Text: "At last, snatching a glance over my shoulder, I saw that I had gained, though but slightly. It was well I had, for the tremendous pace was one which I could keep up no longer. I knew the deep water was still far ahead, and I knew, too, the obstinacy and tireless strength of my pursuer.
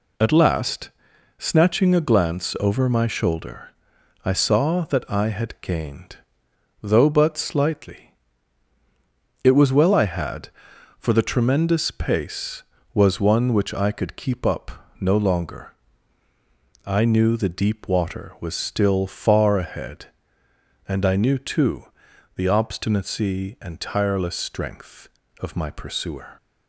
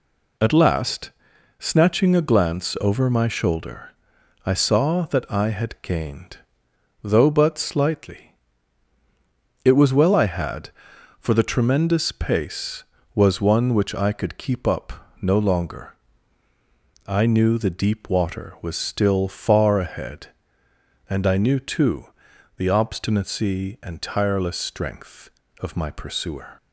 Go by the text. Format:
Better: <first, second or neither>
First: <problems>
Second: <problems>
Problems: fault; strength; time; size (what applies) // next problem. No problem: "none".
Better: neither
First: pauses between "up" and "no"; slight; at 14.7 s; 0.30 s long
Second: pauses between "up" and "no"; slight; at 14.9 s; 0.30 s long